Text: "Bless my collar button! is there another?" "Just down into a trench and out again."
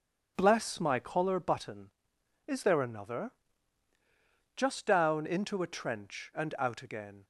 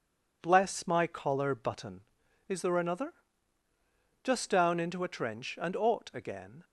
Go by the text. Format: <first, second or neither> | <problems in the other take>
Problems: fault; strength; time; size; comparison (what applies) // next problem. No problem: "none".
first | says "ought" for "out"; at 5.7 s